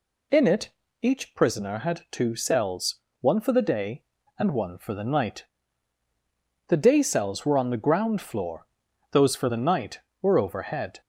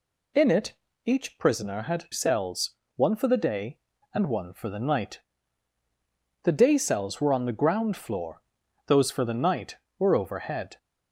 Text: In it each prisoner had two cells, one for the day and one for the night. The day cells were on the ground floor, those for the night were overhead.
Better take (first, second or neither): first